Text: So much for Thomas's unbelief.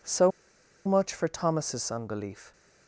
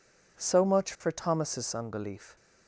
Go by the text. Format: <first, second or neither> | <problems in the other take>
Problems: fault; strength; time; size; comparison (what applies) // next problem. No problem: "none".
second | pauses between "So" and "much"; noticeable; at 0.3 s; 0.57 s long